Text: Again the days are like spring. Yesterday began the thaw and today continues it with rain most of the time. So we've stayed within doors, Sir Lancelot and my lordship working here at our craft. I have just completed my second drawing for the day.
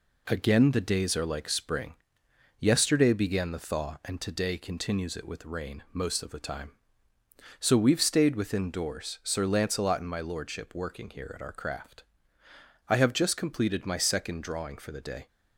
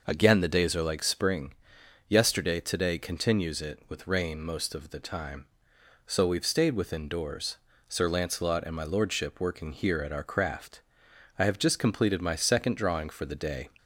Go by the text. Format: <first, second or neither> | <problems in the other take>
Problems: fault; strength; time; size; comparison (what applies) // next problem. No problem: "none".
first | skips "began the thaw and"; at 2.5 s